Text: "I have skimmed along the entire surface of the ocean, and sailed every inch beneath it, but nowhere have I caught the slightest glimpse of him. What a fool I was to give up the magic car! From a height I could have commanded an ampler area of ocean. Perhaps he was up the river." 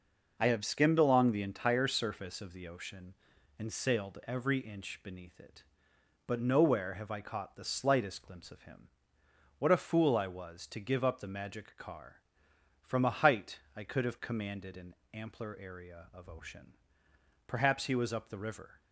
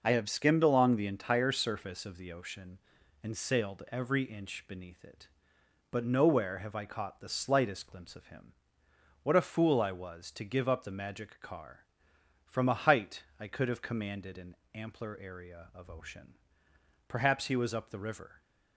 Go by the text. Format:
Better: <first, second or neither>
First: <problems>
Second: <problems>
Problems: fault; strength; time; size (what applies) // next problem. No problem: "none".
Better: neither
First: pauses between "height" and "I"; slight; at 13.5 s; 0.18 s long // pauses between "an" and "ampler"; slight; at 14.9 s; 0.18 s long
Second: pauses between "height" and "I"; slight; at 13.2 s; 0.18 s long // pauses between "an" and "ampler"; slight; at 14.5 s; 0.18 s long